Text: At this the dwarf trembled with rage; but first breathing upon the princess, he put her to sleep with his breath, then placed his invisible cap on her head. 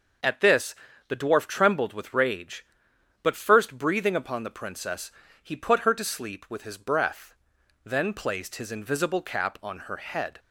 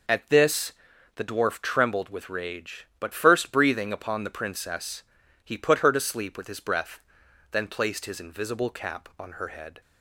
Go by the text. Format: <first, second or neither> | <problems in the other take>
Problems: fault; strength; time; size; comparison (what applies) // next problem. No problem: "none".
neither | pauses between "this" and "the"; the same in both